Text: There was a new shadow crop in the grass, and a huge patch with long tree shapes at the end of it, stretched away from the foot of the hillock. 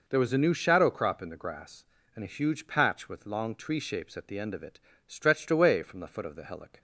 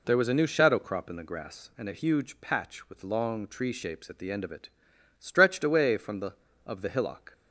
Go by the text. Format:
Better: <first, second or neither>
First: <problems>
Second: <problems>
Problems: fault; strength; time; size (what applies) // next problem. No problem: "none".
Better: first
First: none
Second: skips "foot"; at 6.5 s